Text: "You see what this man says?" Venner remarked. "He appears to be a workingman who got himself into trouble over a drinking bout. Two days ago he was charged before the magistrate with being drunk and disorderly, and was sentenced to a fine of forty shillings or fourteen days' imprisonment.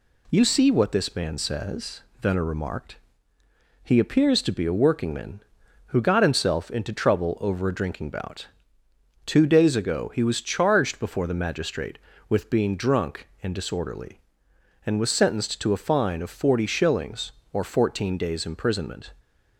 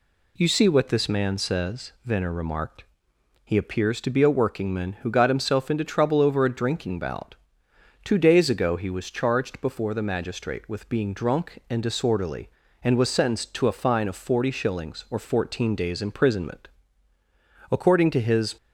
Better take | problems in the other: first | goes on to say "According to his"; noticeable; from 17.7 s on; 0.86 s long

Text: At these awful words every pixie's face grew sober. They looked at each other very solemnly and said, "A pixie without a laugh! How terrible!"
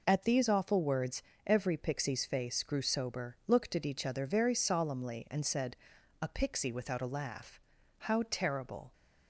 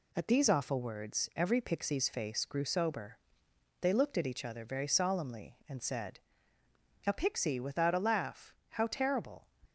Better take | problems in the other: second | pauses between "words" and "every"; slight; at 1.2 s; 0.24 s long // skips "They"; at 3.4 s

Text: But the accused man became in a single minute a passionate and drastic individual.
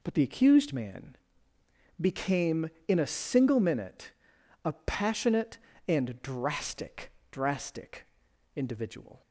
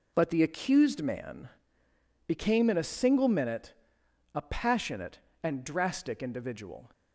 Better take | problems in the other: second | pauses between "man" and "became"; noticeable; at 1.1 s; 0.84 s long; noticeable in the second // pauses between "minute" and "a"; noticeable; at 4.1 s; 0.54 s long; noticeable in the second // says "drastic" twice; at 7.3 s

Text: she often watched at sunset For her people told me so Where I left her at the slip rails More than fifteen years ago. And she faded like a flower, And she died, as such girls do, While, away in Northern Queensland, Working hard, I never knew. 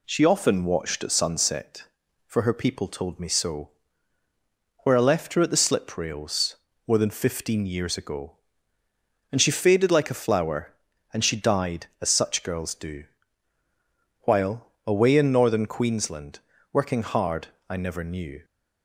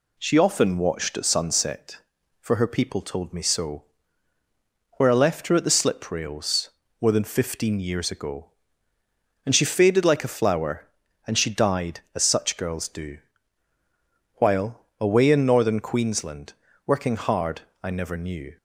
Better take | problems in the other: neither | pauses between "so" and "Where"; the same in both // pauses between "rails" and "More"; slight; the same in both

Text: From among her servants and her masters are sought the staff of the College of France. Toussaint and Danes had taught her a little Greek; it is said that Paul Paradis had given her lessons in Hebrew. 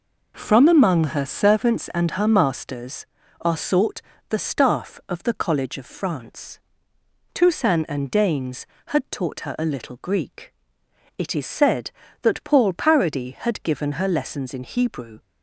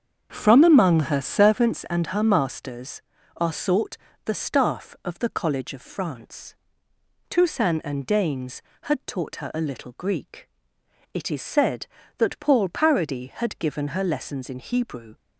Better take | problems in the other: first | starts louder than the rest; strong; until 1.8 s; 7 dB // pauses between "sought" and "the"; slight; at 3.9 s; 0.28 s long; slight in the first

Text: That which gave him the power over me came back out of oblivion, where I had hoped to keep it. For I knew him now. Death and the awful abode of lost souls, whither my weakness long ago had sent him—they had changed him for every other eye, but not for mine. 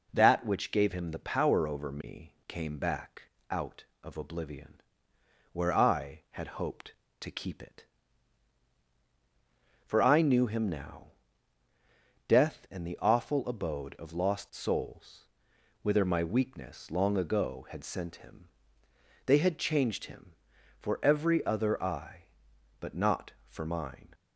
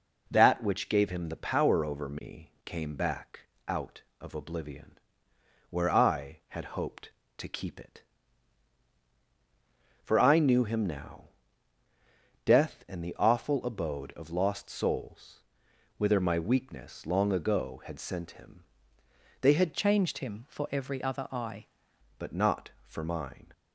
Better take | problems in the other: first | pauses between "back" and "out"; slight; at 3.4 s; 0.26 s long; slight in the first // changes voice from "changed" to "eye"; from 19.7 to 21.6 s; 1.9 s long

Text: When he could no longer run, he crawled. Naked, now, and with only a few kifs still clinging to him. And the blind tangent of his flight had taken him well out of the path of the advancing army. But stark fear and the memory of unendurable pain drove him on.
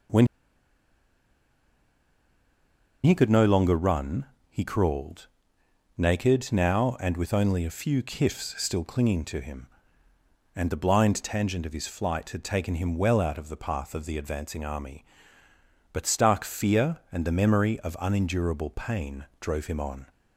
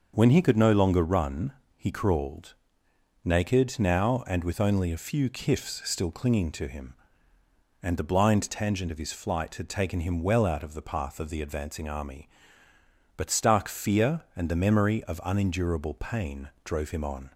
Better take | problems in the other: second | starts louder than the rest; until 3.8 s; 6 dB; also in the second // pauses between "When" and "he"; strong; at 0.2 s; 2.7 s long // pauses between "pain" and "drove"; slight; at 19.2 s; 0.16 s long; slight in the second

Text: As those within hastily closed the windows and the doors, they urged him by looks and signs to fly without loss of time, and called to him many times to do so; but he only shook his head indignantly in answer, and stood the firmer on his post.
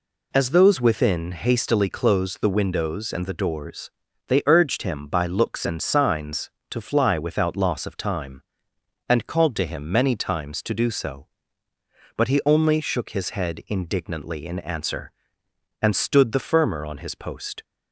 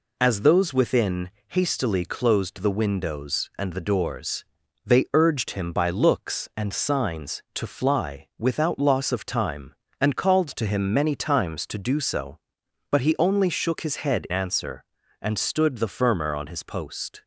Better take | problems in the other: first | pauses between "within" and "hastily"; slight; at 1.2 s; 0.20 s long // skips "indignantly in"; at 14.2 s

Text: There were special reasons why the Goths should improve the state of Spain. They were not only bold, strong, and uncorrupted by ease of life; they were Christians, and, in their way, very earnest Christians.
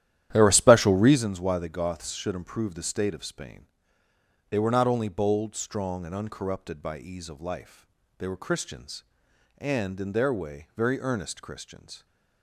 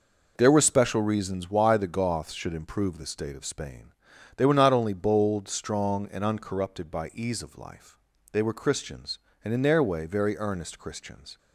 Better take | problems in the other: second | starts louder than the rest; strong; until 1.2 s; 11.5 dB

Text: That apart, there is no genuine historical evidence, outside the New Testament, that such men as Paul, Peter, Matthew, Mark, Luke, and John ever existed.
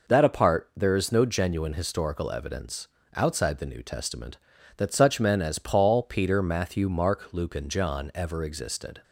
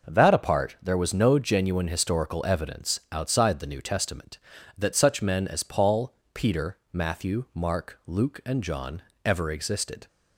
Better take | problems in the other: first | says "was" for "is"; at 0.9 s // pauses between "John" and "ever"; slight; at 9.0 s; 0.22 s long

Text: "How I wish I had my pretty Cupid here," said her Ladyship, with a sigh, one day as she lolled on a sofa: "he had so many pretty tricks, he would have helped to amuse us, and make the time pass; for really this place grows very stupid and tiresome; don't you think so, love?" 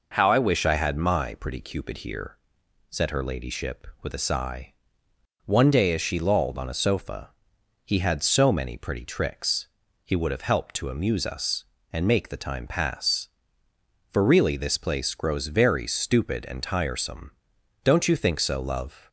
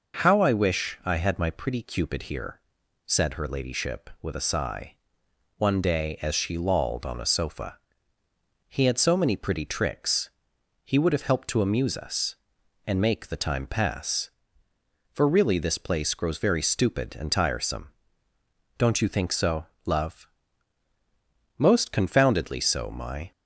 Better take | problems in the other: first | goes on to say "Most confoundedly so my"; strong; from 21.5 s on; 1.7 s long

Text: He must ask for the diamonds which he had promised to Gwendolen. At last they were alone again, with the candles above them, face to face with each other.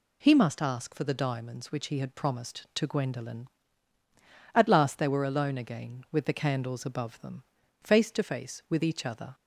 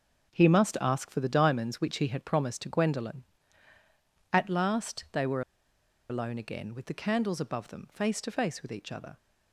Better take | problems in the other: first | starts louder than the rest; until 1.3 s; 6.5 dB // pauses between "were" and "alone"; noticeable; at 5.4 s; 0.68 s long

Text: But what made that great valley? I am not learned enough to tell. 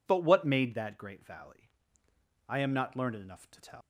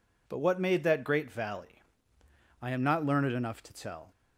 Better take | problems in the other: second | leaves "tell" unfinished; at 3.8 s; 100 ms

